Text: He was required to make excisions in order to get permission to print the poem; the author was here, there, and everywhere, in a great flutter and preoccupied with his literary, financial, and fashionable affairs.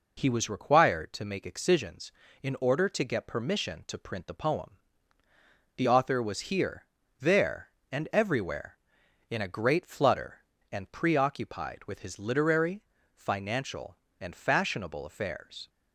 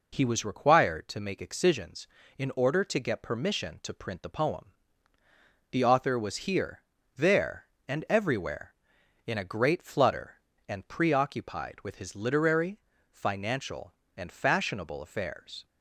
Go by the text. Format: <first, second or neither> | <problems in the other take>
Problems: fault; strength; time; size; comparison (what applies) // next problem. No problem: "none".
neither | none